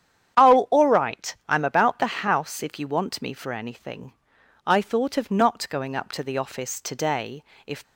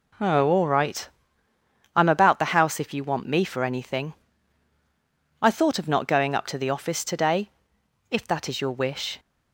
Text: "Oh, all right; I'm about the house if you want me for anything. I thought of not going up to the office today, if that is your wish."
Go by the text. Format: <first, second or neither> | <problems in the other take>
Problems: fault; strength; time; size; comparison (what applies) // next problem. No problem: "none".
second | starts louder than the rest; strong; until 1.5 s; 9.5 dB // stops before "that is your wish"; at 7.8 s